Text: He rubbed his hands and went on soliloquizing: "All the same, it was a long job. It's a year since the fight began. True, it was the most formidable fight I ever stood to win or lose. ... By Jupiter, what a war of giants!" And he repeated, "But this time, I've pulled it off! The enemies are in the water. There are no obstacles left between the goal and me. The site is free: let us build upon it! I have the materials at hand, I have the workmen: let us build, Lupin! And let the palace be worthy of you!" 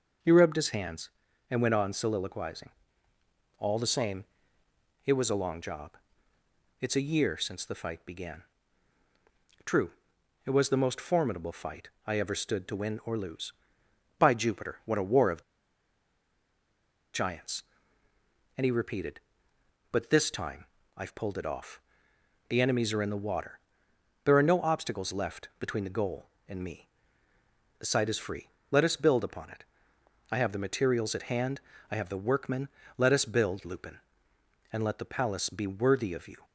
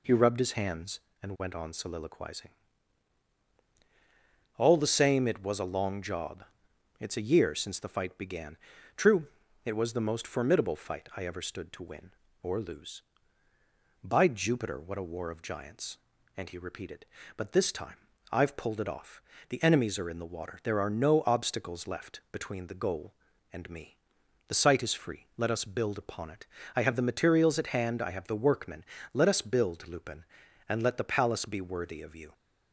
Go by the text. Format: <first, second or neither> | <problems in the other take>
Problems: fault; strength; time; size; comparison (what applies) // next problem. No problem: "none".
second | pauses between "fight" and "I"; slight; at 11.8 s; 0.18 s long // pauses between "of" and "giants"; strong; at 15.4 s; 1.7 s long